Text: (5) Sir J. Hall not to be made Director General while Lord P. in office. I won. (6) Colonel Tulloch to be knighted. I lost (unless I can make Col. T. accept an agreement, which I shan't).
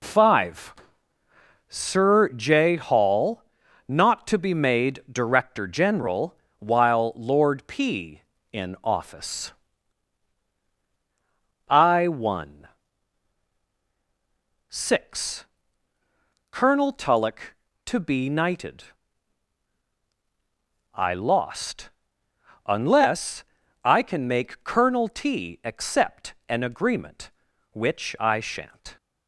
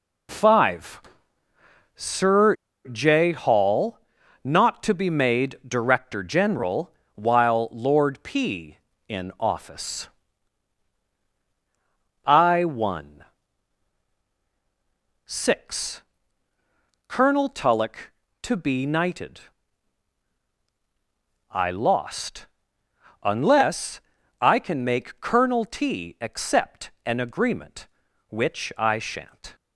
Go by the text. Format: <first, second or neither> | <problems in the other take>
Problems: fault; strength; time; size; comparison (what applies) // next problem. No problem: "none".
first | pauses between "Sir" and "J"; slight; at 2.5 s; 0.35 s long // pauses between "Hall" and "not"; noticeable; at 3.9 s; 0.46 s long; noticeable in the first // pauses between "General" and "while"; slight; at 6.9 s; 0.24 s long; slight in the first // pauses between "unless" and "I"; at 24.0 s; 0.38 s long; also in the first // pauses between "accept" and "an"; slight; at 26.9 s; 0.16 s long; slight in the first